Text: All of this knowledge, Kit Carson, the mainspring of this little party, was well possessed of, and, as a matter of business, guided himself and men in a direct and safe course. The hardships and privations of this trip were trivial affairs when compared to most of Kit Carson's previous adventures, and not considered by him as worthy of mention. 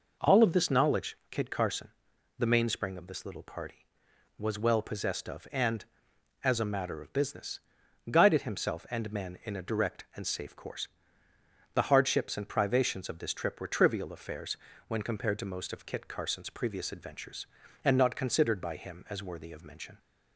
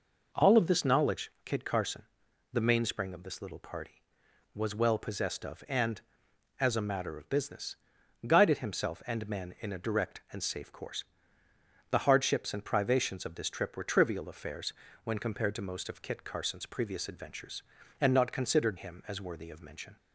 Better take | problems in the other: first | pauses between "affairs" and "when"; slight; at 14.7 s; 0.32 s long; slight in the first // skips "by"; at 18.7 s

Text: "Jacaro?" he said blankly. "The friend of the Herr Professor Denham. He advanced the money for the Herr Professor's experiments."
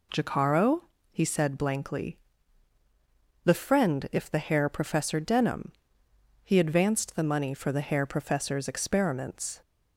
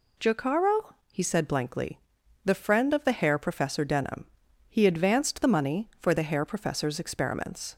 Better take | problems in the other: second | says "if" for "of"; at 4.1 s

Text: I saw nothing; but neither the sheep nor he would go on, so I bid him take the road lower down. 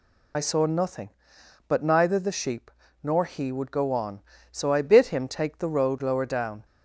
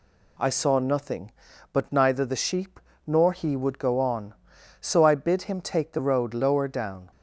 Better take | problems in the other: second | loses the start of "I"; at 0.3 s; 30 ms // pauses between "sheep" and "nor"; slight; at 2.7 s; 0.32 s long; slight in the second

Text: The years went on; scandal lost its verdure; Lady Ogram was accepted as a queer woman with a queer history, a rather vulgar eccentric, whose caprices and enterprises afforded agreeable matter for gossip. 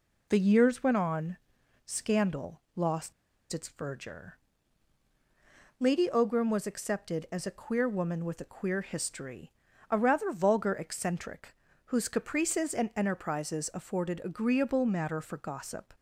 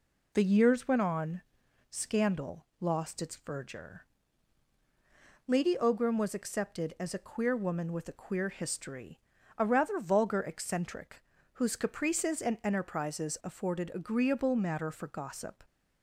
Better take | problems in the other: second | pauses between "scandal" and "lost"; slight; at 2.5 s; 0.16 s long; slight in the second // pauses between "lost" and "its"; at 3.1 s; 0.39 s long

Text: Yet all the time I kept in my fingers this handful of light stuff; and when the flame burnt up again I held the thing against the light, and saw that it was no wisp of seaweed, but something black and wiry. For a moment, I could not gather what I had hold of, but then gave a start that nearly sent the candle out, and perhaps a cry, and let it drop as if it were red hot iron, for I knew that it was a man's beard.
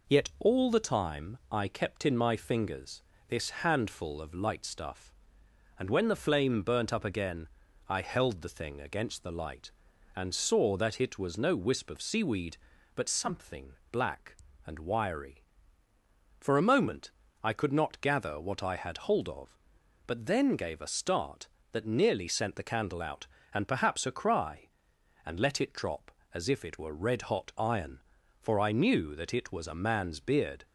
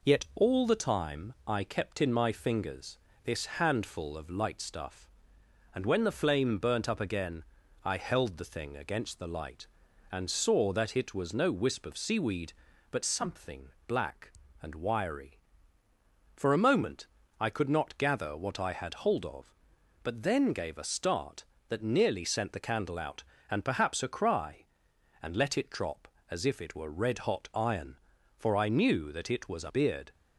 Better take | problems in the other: first | pauses between "fingers" and "this"; slight; at 2.9 s; 0.26 s long; slight in the first // pauses between "again" and "I"; at 7.4 s; 0.40 s long; also in the first // pauses between "something" and "black"; slight; at 13.6 s; 0.16 s long; slight in the first // skips "man's"; at 29.6 s

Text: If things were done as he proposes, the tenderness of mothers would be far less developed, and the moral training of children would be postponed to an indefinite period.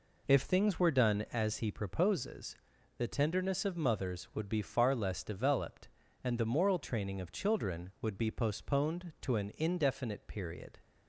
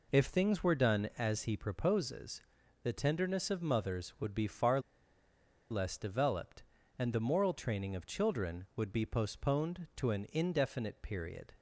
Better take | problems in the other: first | pauses between "far" and "less"; noticeable; at 4.7 s; 0.90 s long

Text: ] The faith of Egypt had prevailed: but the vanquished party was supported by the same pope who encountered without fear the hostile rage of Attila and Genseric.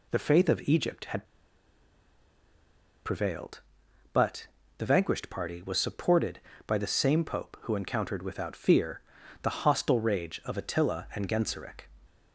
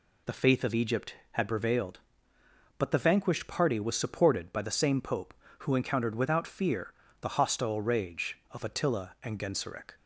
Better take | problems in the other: second | pauses between "had" and "prevailed"; strong; at 1.2 s; 1.8 s long // pauses between "but" and "the"; slight; at 4.4 s; 0.28 s long // pauses between "fear" and "the"; at 8.9 s; 0.42 s long; slight in the second

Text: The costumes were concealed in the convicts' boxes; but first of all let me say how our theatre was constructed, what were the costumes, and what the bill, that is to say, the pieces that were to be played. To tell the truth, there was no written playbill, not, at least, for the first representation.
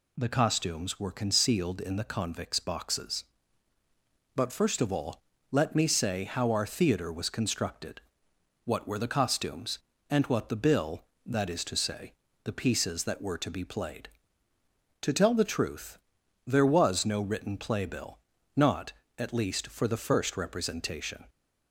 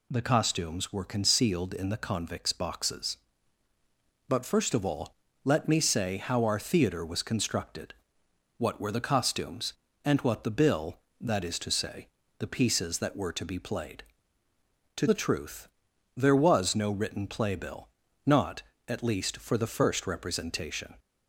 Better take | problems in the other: first | pauses between "all" and "let"; slight; at 5.1 s; 0.28 s long; slight in the first // skips "tell"; at 15.0 s

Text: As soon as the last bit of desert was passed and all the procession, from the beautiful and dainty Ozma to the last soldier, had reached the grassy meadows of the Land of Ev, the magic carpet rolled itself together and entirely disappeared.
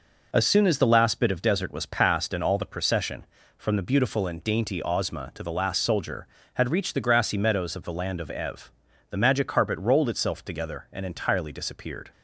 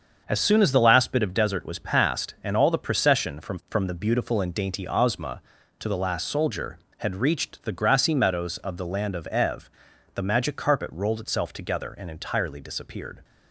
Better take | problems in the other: first | starts louder than the rest; until 1.2 s; 6.5 dB // says "from" twice; at 3.6 s

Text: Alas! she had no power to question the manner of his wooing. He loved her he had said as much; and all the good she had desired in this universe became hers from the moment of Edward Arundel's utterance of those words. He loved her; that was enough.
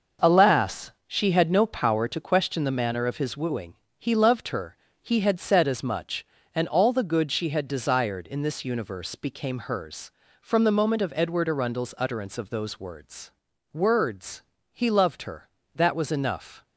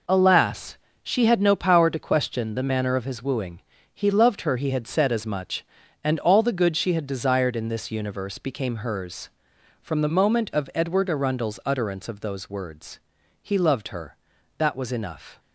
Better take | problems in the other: second | starts louder than the rest; until 1.4 s; 6 dB // pauses between "her" and "he"; slight; at 4.7 s; 0.26 s long // says "words" twice; at 13.7 s

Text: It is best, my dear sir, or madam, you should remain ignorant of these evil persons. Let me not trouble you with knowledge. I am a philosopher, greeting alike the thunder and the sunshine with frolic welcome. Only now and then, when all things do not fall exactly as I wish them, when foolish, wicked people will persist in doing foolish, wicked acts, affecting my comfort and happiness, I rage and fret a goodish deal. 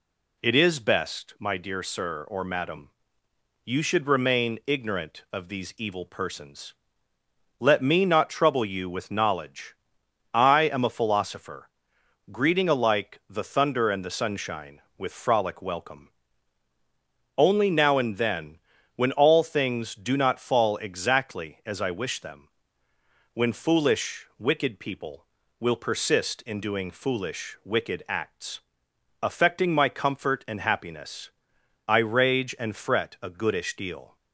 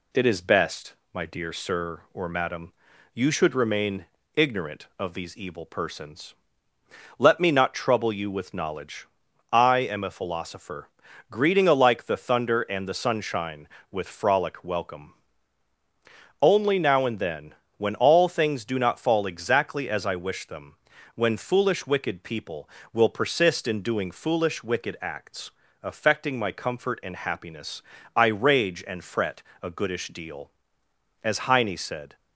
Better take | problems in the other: first | pauses between "remain" and "ignorant"; slight; at 4.0 s; 0.32 s long // pauses between "fret" and "a"; slight; at 29.4 s; 0.22 s long // goes on to say "As Heine said"; noticeable; from 31.2 s on; 0.92 s long

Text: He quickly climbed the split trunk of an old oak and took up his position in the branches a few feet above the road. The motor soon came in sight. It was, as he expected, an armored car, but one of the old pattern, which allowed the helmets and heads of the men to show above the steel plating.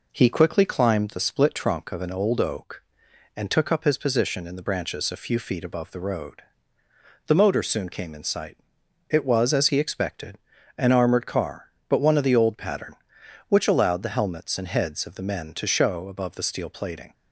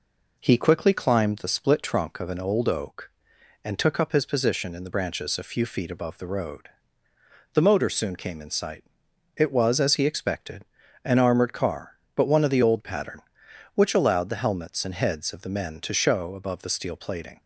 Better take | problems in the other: neither | none

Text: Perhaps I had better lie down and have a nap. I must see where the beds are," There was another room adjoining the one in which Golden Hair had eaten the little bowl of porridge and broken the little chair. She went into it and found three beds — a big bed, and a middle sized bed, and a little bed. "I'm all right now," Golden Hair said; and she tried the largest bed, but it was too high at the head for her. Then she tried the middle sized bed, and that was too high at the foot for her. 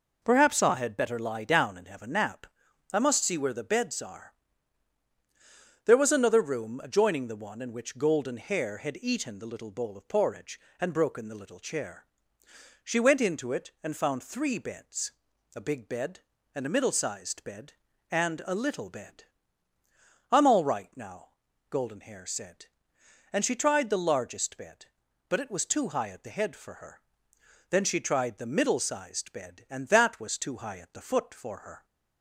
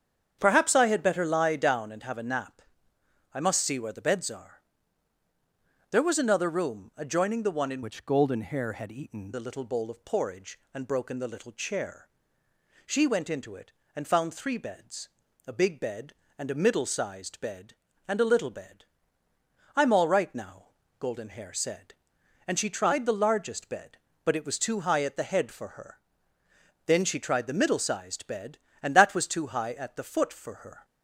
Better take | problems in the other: first | starts louder than the rest; strong; until 1.4 s; 8 dB // changes voice from "which" to "eaten"; from 7.8 to 9.3 s; 1.5 s long

